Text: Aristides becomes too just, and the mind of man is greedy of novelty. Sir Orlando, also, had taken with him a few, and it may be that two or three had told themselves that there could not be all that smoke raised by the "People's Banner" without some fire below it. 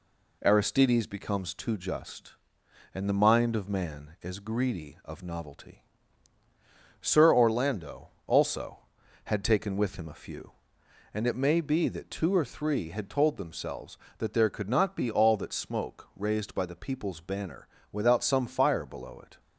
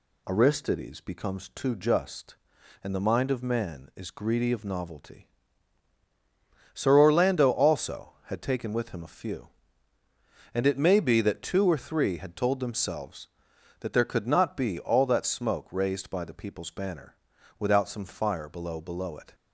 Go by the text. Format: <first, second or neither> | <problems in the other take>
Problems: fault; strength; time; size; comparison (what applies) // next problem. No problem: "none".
first | pauses between "Banner" and "without"; at 17.1 s; 0.44 s long; slight in the first // says "below" twice; at 18.8 s